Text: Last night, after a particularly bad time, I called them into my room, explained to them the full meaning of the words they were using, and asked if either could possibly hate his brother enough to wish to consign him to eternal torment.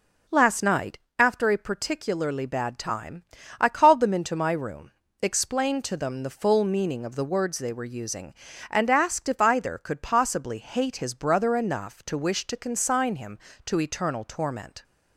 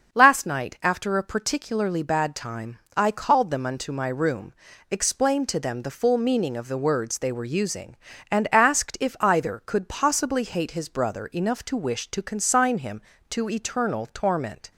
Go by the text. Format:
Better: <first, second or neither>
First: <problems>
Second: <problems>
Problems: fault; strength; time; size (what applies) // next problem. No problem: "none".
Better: first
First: none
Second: starts louder than the rest; until 1.1 s; 6.5 dB // says "unto" for "into"; at 3.6 s